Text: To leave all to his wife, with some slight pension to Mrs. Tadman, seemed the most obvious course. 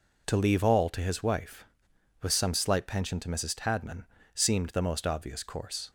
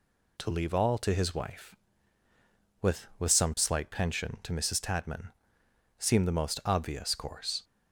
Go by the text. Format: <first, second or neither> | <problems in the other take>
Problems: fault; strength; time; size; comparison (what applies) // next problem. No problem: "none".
first | says "with" twice; at 3.1 s